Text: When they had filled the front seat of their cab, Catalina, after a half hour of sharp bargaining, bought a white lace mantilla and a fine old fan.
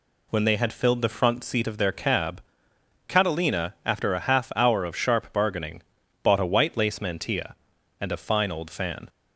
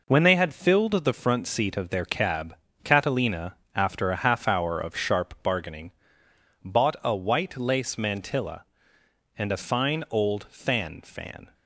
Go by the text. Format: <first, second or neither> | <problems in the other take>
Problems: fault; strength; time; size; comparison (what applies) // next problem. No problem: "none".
first | says "fan" twice; at 11.0 s